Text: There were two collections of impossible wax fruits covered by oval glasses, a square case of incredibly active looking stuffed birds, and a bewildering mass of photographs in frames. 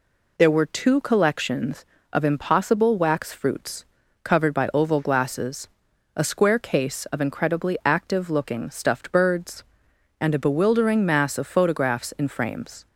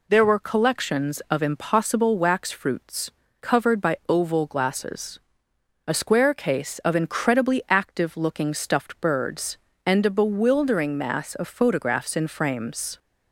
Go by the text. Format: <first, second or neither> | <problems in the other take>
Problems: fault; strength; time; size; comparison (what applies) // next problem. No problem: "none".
first | skips "two"; at 0.3 s // pauses between "fruits" and "covered"; slight; at 3.1 s; 0.30 s long; also in the first